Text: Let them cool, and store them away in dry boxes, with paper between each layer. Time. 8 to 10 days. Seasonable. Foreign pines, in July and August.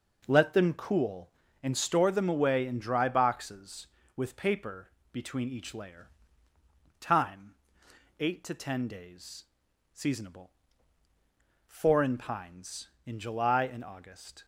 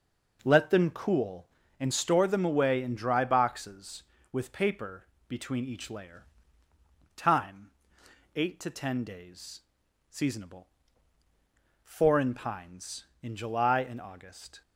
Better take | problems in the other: neither | pauses between "paper" and "between"; slight; the same in both

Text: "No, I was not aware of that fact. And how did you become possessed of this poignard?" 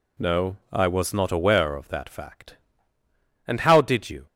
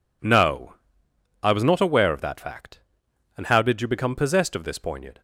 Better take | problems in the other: second | stops before "become possessed of this poignard"; at 4.2 s

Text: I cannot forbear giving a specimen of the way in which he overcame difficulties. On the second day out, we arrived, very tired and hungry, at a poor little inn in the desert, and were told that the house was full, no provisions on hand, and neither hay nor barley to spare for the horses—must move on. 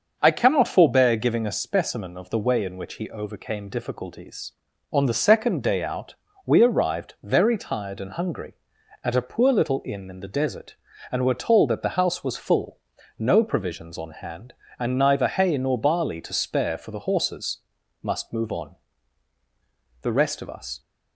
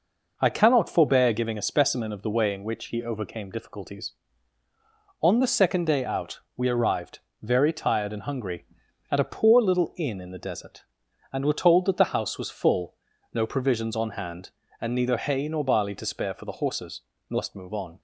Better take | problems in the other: second | starts louder than the rest; until 1.2 s; 6.5 dB // goes on to say "The rest of us"; noticeable; from 20.0 s on; 0.78 s long

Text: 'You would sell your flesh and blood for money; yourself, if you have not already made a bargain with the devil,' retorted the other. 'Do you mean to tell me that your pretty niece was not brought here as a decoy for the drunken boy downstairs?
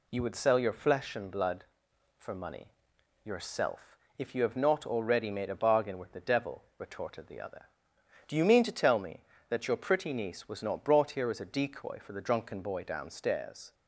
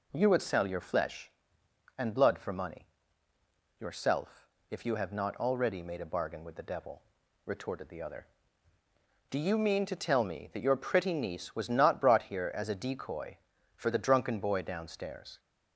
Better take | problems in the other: neither | none

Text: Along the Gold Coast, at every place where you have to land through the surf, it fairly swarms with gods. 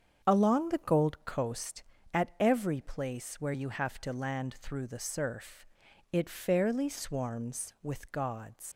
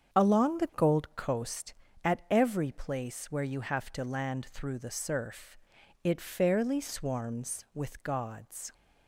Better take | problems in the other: second | starts louder than the rest; strong; until 1.3 s; 7.5 dB; strong in the second // leaves "gods" unfinished; at 8.7 s; 95 ms

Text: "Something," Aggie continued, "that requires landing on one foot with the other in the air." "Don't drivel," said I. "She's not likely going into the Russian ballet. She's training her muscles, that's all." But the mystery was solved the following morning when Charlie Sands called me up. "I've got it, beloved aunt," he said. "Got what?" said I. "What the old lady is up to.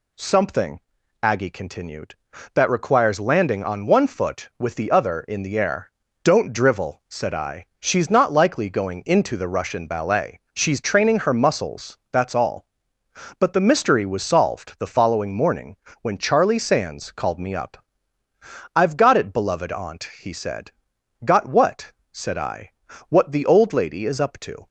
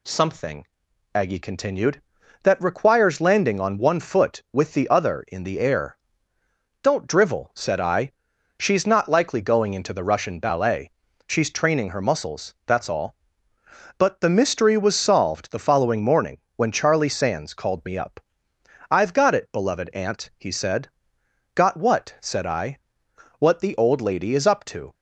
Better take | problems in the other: neither | pauses between "morning" and "when"; slight; the same in both

